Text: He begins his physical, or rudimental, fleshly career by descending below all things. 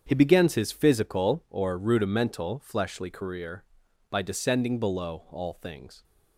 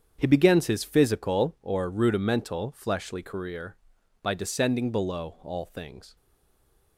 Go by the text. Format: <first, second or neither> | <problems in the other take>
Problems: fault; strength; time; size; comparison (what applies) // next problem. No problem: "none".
first | starts louder than the rest; strong; until 1.2 s; 8 dB; strong in the first // stays silent after the last word; slight; from 6.1 s on; 0.8 s long